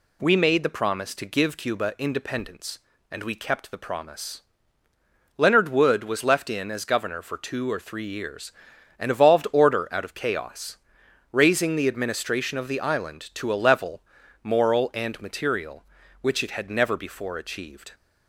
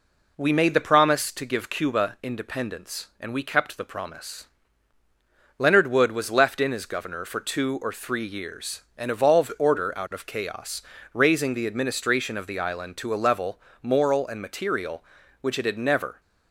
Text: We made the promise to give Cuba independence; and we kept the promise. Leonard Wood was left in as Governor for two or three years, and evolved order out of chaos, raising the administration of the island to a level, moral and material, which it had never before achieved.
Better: first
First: none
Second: stops before "before achieved"; at 16.1 s

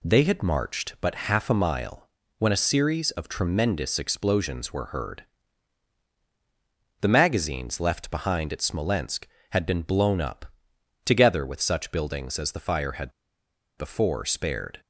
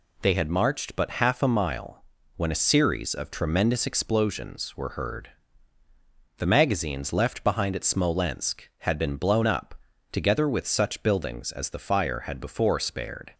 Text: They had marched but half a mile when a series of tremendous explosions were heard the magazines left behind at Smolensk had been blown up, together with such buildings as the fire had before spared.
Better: second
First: pauses between "mile" and "when"; slight; at 2.0 s; 0.30 s long // pauses between "heard" and "the"; strong; at 5.2 s; 1.7 s long // pauses between "had" and "before"; noticeable; at 13.1 s; 0.67 s long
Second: pauses between "mile" and "when"; slight; at 2.0 s; 0.32 s long // pauses between "heard" and "the"; at 5.2 s; 1.0 s long

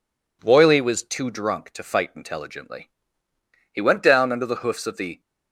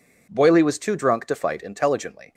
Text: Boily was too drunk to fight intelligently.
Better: second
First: goes on to say "He went down under the hoofs of the"; from 3.7 s on; 1.4 s long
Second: none

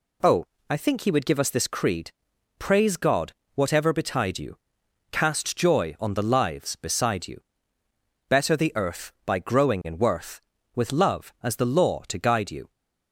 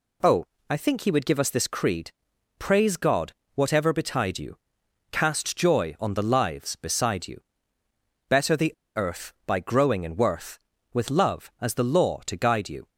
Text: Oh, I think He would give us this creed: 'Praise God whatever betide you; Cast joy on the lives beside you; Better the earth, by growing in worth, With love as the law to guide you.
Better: first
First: pauses between "God" and "whatever"; slight; at 3.3 s; 0.22 s long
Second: pauses between "God" and "whatever"; slight; at 3.3 s; 0.22 s long // pauses between "the" and "earth"; slight; at 8.7 s; 0.24 s long

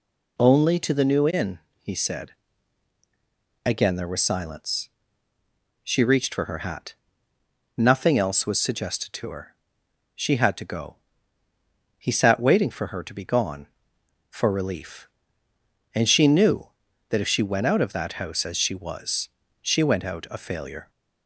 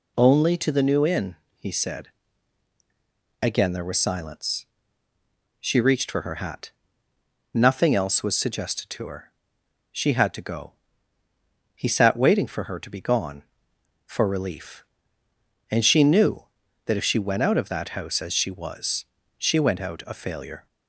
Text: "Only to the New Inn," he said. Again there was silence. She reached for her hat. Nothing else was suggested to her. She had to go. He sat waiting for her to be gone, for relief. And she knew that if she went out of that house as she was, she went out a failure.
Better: neither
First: none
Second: none

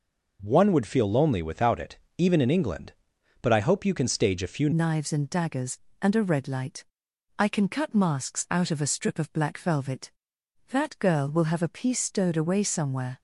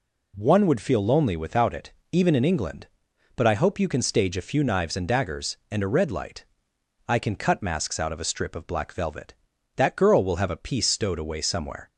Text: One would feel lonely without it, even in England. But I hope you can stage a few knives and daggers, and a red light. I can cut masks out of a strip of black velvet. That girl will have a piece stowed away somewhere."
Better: second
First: changes voice at "knives"; from 4.7 s on; 8.4 s long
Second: none

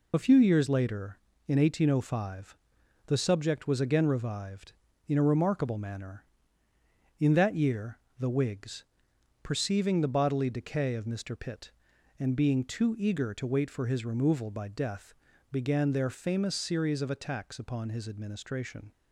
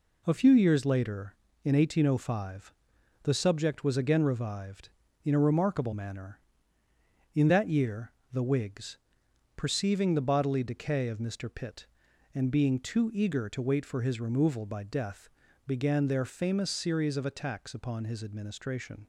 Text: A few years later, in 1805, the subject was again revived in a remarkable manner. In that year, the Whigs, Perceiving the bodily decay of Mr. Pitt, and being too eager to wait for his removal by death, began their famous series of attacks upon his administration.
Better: second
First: loses the start of "A"; at 0.1 s; 35 ms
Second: none

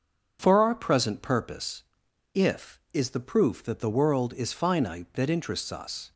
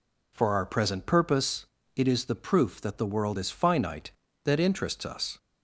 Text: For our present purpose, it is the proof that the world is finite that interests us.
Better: second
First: starts louder than the rest; strong; until 1.4 s; 7.5 dB // says "if" for "it"; at 2.3 s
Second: none

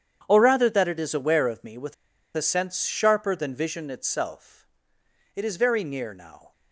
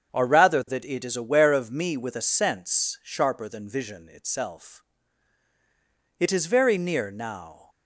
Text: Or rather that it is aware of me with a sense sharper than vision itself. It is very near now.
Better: second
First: starts louder than the rest; strong; until 1.2 s; 8.5 dB // pauses between "with" and "a"; at 1.9 s; 0.41 s long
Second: starts louder than the rest; strong; until 1.1 s; 7.5 dB

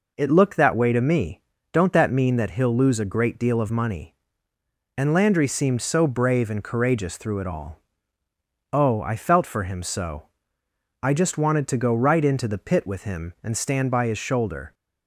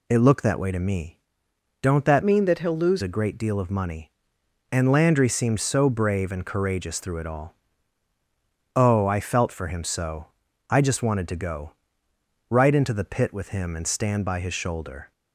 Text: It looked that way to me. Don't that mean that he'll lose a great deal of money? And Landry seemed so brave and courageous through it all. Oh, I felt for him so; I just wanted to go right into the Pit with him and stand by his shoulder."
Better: first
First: none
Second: changes voice from "mean" to "lose"; from 2.2 to 3.0 s; 0.8 s long // pauses between "go" and "right"; noticeable; at 11.7 s; 0.76 s long

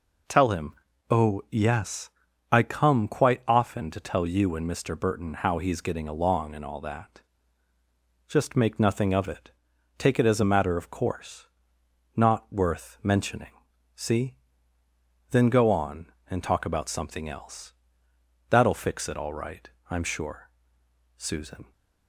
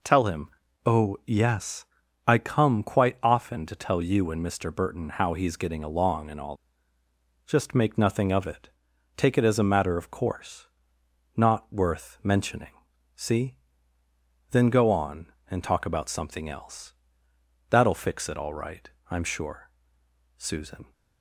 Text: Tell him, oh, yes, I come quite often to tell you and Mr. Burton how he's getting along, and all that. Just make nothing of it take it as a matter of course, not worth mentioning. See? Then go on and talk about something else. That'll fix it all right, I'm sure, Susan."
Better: first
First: pauses between "it" and "take"; noticeable; at 9.4 s; 0.46 s long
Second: skips "that"; at 7.0 s // pauses between "it" and "take"; noticeable; at 8.6 s; 0.46 s long

